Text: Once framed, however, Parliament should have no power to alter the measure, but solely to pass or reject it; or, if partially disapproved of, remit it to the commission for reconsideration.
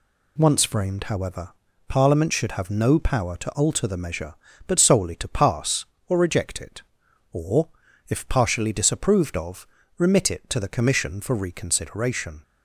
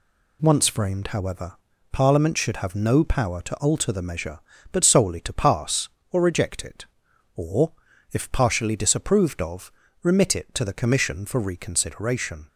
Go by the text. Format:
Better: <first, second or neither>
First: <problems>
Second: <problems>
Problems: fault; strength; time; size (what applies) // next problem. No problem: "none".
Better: neither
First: none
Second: none